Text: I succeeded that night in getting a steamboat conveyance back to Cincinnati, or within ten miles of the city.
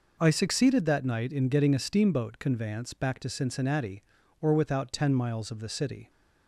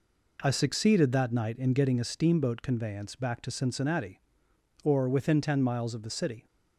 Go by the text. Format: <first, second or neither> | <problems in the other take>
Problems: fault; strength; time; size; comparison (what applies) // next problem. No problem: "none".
second | says "without" for "within"; at 4.5 s